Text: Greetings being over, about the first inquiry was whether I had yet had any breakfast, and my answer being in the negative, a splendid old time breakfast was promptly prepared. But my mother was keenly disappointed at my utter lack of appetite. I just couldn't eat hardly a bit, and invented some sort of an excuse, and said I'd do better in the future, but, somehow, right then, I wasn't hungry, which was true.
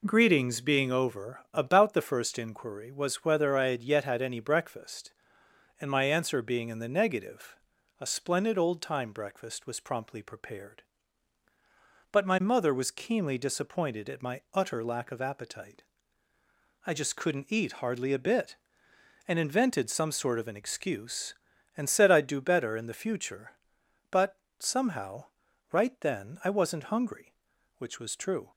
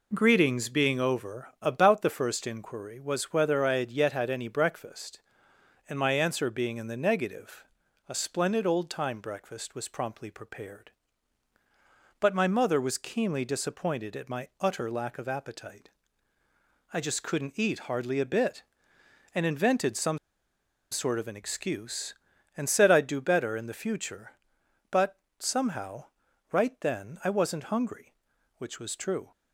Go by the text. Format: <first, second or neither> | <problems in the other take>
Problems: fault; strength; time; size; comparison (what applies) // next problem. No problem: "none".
first | pauses between "some" and "sort"; noticeable; at 20.1 s; 0.73 s long